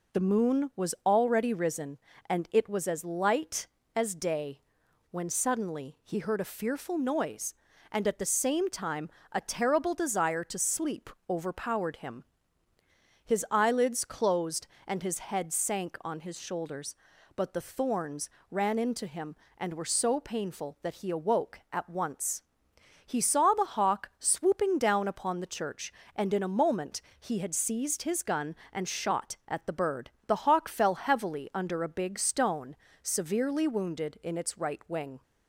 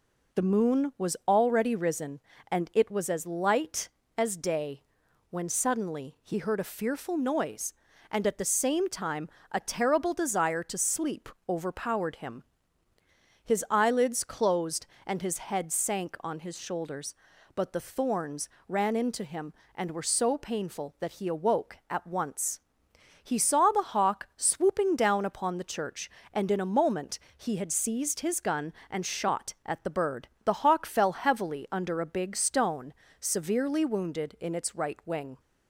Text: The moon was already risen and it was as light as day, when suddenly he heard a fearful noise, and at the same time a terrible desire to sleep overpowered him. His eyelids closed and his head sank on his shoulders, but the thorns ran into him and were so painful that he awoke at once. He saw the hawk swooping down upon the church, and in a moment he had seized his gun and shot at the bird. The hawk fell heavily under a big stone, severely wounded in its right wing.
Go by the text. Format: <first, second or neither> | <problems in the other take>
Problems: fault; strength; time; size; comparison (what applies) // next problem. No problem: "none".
neither | pauses between "time" and "a"; slight; the same in both // pauses between "sleep" and "overpowered"; slight; the same in both // pauses between "thorns" and "ran"; slight; the same in both // pauses between "moment" and "he"; slight; the same in both